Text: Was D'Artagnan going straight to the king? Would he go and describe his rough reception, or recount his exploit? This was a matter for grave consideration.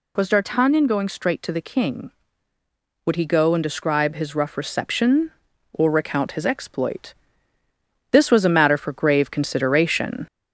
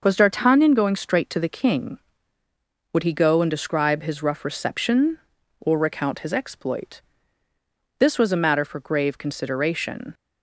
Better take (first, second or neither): second